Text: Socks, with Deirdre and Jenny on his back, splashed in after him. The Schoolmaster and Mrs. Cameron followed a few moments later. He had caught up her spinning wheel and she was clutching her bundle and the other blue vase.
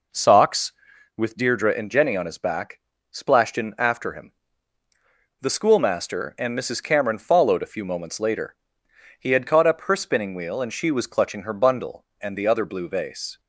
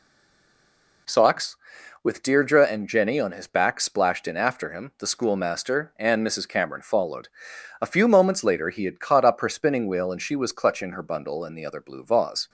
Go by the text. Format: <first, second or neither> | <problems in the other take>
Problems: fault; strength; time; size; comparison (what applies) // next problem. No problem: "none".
first | stays silent before the first word; until 1.0 s; 1.0 s long // pauses between "followed" and "a"; noticeable; at 7.2 s; 0.50 s long